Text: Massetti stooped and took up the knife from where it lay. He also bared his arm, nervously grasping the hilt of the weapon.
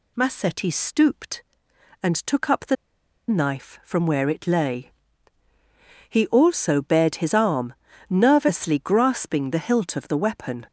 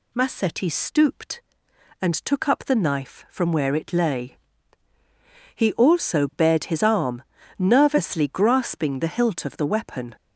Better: second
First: pauses between "the" and "knife"; noticeable; at 2.7 s; 0.53 s long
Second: none

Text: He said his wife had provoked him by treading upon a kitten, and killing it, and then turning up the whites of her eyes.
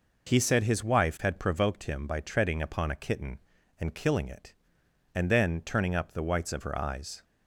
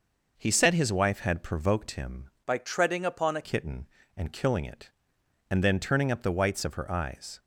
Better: first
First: none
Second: changes voice from "by" to "a"; from 2.4 to 3.4 s; 1.0 s long

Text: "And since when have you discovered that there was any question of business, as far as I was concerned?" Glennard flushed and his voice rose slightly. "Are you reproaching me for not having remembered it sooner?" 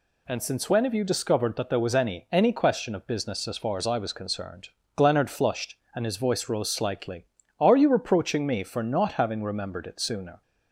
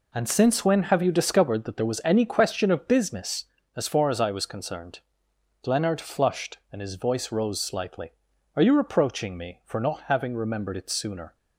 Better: second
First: says "any" twice; at 2.3 s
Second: none

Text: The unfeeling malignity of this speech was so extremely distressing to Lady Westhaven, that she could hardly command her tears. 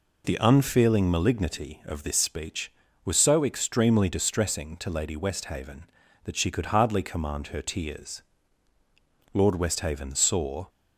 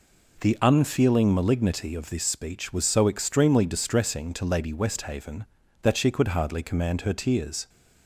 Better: second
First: goes on to say "Lord Westhaven saw"; from 9.3 s on; 1.3 s long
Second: none

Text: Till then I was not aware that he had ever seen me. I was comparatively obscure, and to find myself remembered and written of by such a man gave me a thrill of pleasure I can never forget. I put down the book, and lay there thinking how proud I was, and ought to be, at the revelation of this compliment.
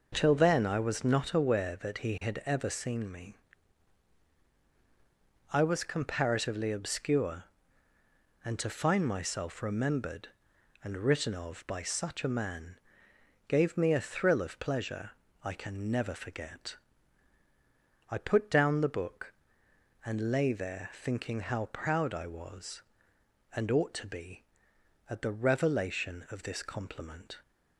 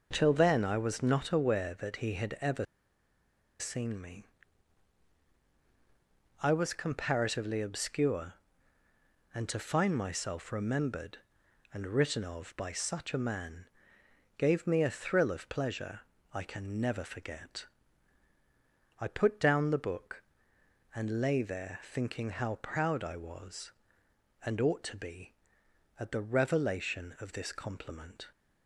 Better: first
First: pauses between "man" and "gave"; noticeable; at 12.7 s; 0.70 s long // pauses between "pleasure" and "I"; slight; at 15.1 s; 0.34 s long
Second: pauses between "ever" and "seen"; noticeable; at 2.6 s; 0.94 s long // pauses between "man" and "gave"; noticeable; at 13.6 s; 0.70 s long // pauses between "pleasure" and "I"; slight; at 15.9 s; 0.34 s long

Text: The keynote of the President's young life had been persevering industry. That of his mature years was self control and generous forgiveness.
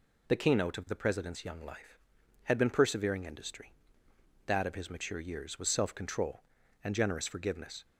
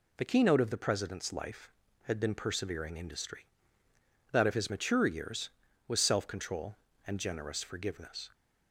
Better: first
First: none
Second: skips "young"; at 1.3 s

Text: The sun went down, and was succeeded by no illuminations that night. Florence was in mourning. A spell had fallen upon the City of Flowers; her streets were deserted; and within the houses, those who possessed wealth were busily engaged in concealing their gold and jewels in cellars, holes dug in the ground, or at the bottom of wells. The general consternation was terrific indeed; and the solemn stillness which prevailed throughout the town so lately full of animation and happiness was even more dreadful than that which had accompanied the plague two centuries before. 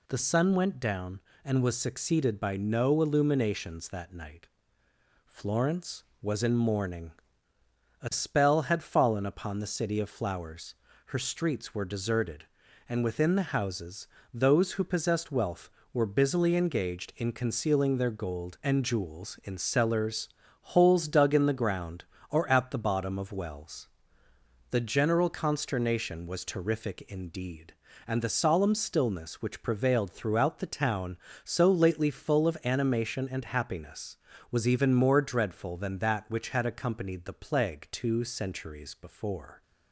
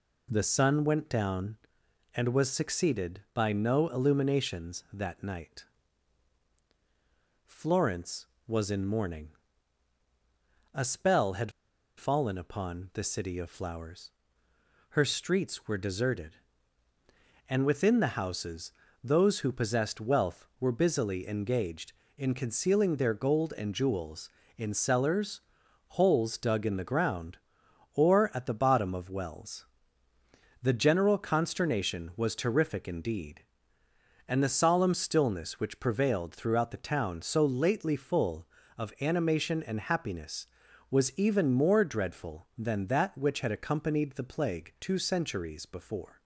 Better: first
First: none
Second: pauses between "had" and "fallen"; noticeable; at 11.5 s; 0.46 s long

